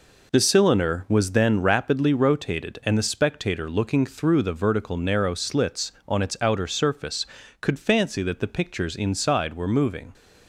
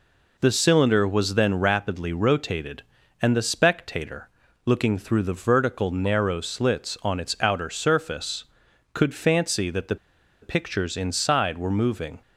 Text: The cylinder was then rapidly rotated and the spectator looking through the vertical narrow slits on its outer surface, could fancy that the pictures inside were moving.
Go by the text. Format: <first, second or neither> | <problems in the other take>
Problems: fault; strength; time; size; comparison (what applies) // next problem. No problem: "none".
first | pauses between "spectator" and "looking"; slight; at 4.2 s; 0.36 s long // pauses between "the" and "pictures"; noticeable; at 9.9 s; 0.46 s long